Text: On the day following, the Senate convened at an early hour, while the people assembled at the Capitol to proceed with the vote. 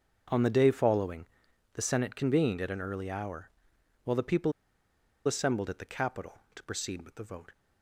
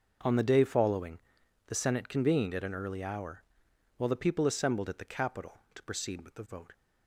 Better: second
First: starts louder than the rest; until 1.7 s; 6.5 dB // pauses between "people" and "assembled"; noticeable; at 4.5 s; 0.74 s long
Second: starts louder than the rest; until 1.7 s; 6 dB

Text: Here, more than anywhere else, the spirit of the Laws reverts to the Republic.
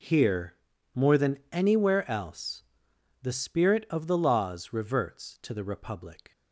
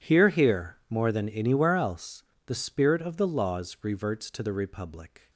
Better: first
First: none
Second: says "Here" twice; at 0.2 s

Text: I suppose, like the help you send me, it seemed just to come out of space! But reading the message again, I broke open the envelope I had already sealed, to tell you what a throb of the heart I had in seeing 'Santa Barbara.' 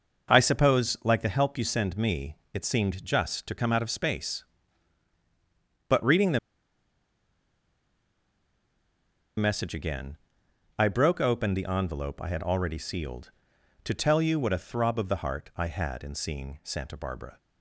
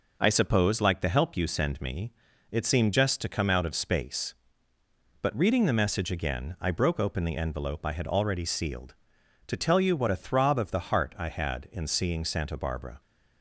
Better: second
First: pauses between "the" and "message"; strong; at 6.3 s; 2.9 s long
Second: none

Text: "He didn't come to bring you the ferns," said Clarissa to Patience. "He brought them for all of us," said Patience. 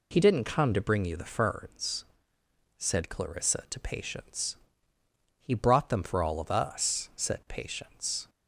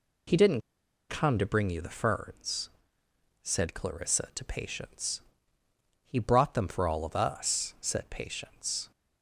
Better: first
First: none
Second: pauses between "didn't" and "come"; noticeable; at 0.6 s; 0.49 s long

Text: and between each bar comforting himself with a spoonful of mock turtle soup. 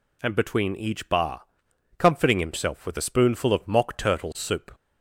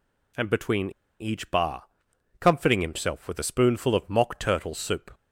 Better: first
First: pauses between "bar" and "comforting"; noticeable; at 1.4 s; 0.56 s long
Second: pauses between "between" and "each"; slight; at 0.8 s; 0.30 s long // pauses between "bar" and "comforting"; noticeable; at 1.8 s; 0.56 s long

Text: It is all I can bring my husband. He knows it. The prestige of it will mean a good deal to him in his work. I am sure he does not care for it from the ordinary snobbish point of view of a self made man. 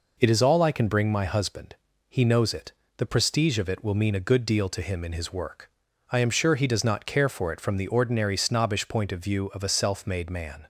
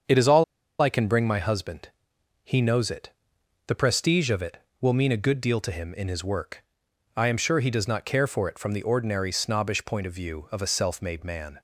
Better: first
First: none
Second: starts louder than the rest; until 1.4 s; 7 dB // pauses between "all" and "I"; slight; at 0.4 s; 0.35 s long

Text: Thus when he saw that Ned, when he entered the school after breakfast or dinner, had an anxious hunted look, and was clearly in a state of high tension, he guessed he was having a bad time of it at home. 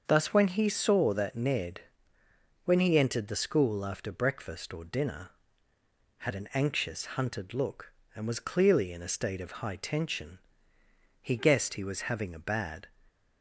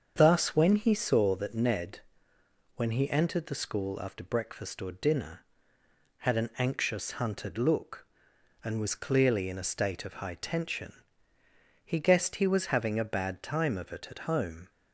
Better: second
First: starts louder than the rest; until 1.0 s; 6.5 dB // stops before "time of it at home"; at 13.0 s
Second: starts louder than the rest; until 1.1 s; 7 dB

